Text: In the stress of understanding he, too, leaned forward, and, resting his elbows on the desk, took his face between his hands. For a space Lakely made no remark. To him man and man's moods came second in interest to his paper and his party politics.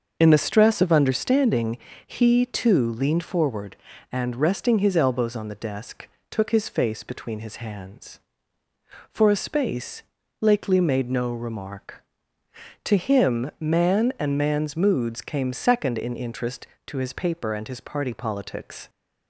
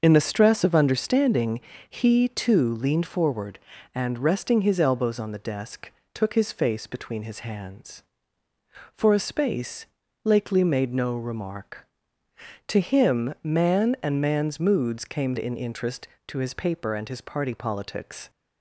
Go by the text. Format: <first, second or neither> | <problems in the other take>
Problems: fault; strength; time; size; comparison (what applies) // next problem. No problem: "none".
first | starts louder than the rest; until 1.0 s; 6.5 dB; also in the first // pauses between "understanding" and "he"; slight; at 1.5 s; 0.30 s long; slight in the first // pauses between "space" and "Lakely"; slight; at 9.8 s; 0.36 s long; slight in the first // skips "second"; at 15.3 s